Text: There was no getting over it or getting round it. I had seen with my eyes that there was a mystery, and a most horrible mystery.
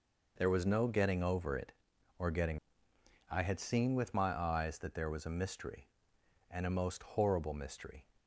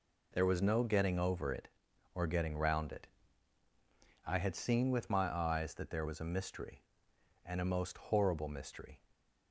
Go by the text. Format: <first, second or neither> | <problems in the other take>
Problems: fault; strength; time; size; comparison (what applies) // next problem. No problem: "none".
second | skips "round it"; at 2.9 s